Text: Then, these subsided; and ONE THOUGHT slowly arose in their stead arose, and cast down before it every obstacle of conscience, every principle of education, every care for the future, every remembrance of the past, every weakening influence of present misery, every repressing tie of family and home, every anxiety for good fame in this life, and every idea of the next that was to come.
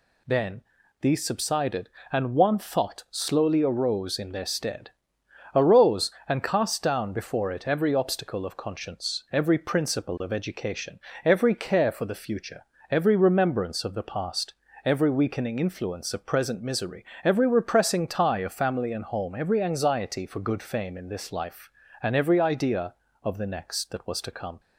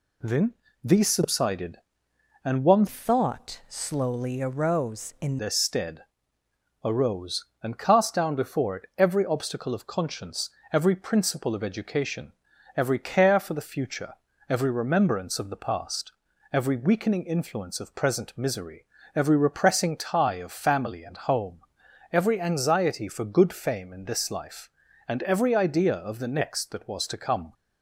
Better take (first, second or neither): first